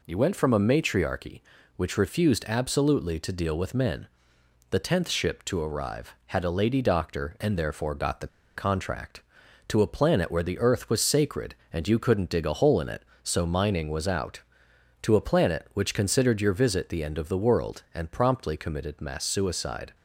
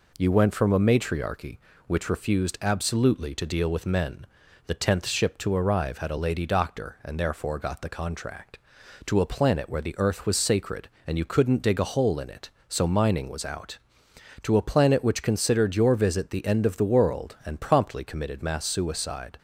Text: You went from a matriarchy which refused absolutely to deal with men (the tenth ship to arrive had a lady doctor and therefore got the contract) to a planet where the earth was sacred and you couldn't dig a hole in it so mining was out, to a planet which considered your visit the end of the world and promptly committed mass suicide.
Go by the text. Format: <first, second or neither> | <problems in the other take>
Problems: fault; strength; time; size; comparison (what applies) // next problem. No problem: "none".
second | pauses between "the" and "contract"; slight; at 8.2 s; 0.29 s long